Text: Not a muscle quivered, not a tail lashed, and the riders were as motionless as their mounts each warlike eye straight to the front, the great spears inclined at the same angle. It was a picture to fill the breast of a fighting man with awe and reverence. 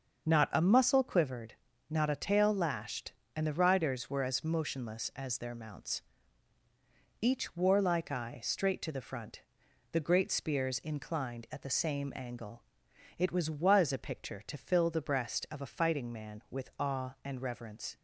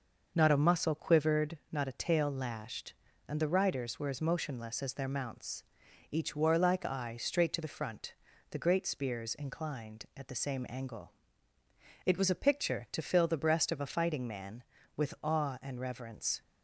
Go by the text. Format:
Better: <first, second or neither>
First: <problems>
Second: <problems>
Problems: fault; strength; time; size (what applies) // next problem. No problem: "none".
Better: second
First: starts louder than the rest; until 1.3 s; 6.5 dB // pauses between "mounts" and "each"; at 6.0 s; 1.2 s long // says "was" twice; at 13.4 s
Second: starts louder than the rest; noticeable; until 1.3 s; 6 dB // pauses between "mounts" and "each"; noticeable; at 5.6 s; 0.48 s long